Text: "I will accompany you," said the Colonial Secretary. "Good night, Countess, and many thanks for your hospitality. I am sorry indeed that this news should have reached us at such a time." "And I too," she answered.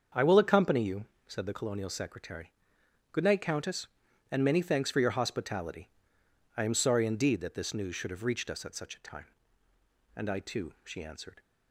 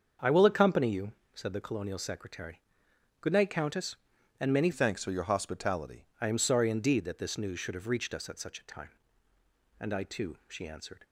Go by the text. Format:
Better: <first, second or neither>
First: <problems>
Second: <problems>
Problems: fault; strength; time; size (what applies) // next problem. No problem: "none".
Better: first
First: starts louder than the rest; until 1.3 s; 6.5 dB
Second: starts louder than the rest; until 1.4 s; 6.5 dB // changes voice from "thanks" to "hospitality"; from 4.7 to 6.0 s; 1.3 s long